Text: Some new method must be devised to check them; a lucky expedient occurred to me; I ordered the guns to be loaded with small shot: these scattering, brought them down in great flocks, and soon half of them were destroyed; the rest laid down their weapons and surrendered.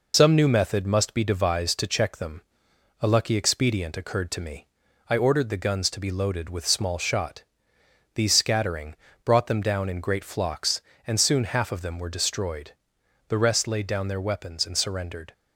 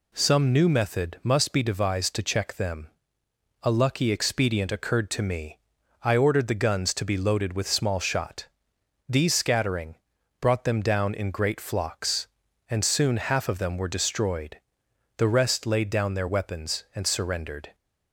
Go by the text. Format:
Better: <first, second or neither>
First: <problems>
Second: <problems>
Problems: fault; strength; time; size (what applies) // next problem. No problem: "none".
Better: second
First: loses the start of "Some"; at 0.1 s; 45 ms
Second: none